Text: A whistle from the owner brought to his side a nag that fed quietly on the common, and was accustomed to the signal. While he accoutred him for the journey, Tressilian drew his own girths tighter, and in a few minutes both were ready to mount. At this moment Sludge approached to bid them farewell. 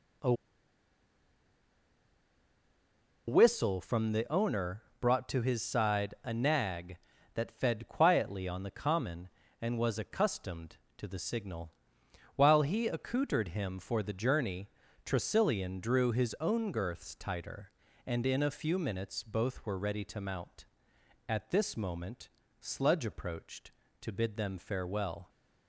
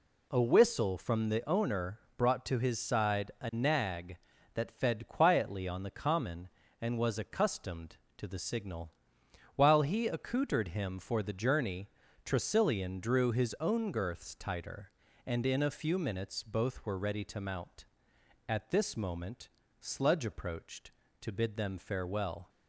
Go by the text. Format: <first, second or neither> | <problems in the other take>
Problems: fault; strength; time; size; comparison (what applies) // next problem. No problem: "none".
second | pauses between "A" and "whistle"; strong; at 0.3 s; 2.9 s long // pauses between "owner" and "brought"; slight; at 4.8 s; 0.18 s long; slight in the second // pauses between "moment" and "Sludge"; slight; at 22.2 s; 0.32 s long; slight in the second